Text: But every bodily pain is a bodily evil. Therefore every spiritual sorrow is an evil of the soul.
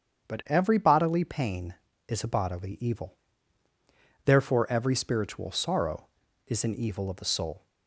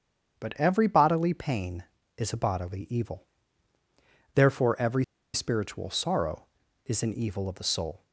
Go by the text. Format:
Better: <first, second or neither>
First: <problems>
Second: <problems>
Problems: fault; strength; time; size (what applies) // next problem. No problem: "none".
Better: first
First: starts louder than the rest; strong; until 1.3 s; 8 dB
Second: starts louder than the rest; strong; until 1.4 s; 8 dB // pauses between "every" and "spiritual"; slight; at 5.0 s; 0.29 s long